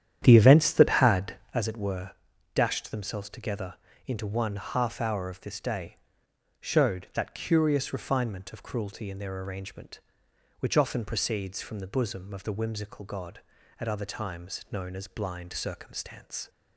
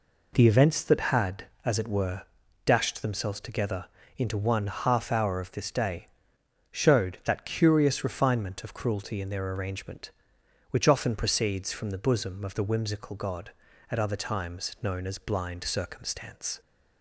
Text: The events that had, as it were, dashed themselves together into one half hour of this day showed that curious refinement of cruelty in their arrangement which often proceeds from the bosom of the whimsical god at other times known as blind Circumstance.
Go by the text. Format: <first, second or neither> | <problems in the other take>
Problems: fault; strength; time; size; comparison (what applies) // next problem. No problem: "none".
second | starts louder than the rest; strong; until 1.6 s; 10 dB // pauses between "together" and "into"; slight; at 3.7 s; 0.30 s long; slight in the second // pauses between "day" and "showed"; noticeable; at 5.9 s; 0.64 s long; noticeable in the second